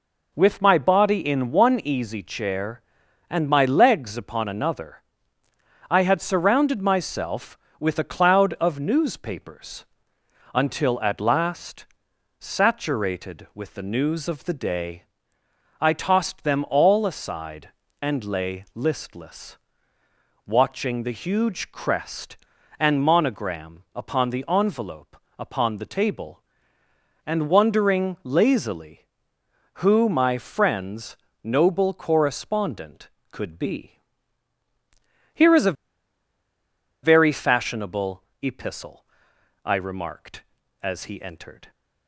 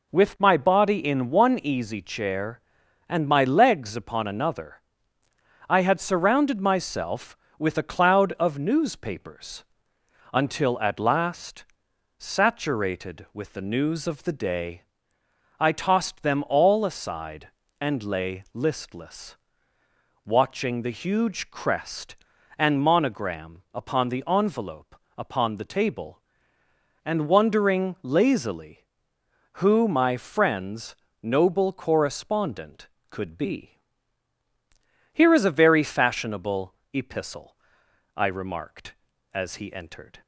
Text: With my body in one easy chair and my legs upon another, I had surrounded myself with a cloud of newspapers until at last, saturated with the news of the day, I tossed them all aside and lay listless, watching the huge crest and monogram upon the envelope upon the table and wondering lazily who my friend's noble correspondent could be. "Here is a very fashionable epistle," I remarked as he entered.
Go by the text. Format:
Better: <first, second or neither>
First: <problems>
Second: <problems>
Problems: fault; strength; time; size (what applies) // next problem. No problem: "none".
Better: second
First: pauses between "newspapers" and "until"; noticeable; at 9.8 s; 0.70 s long // pauses between "envelope" and "upon"; slight; at 25.1 s; 0.24 s long // pauses between "friend's" and "noble"; slight; at 31.1 s; 0.26 s long // pauses between "a" and "very"; strong; at 35.7 s; 1.3 s long // pauses between "fashionable" and "epistle"; slight; at 38.2 s; 0.20 s long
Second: pauses between "newspapers" and "until"; noticeable; at 9.6 s; 0.70 s long // pauses between "envelope" and "upon"; slight; at 24.9 s; 0.24 s long // pauses between "friend's" and "noble"; slight; at 30.9 s; 0.26 s long // pauses between "fashionable" and "epistle"; slight; at 36.7 s; 0.20 s long